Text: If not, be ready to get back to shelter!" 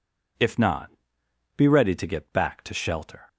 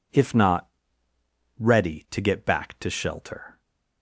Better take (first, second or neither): first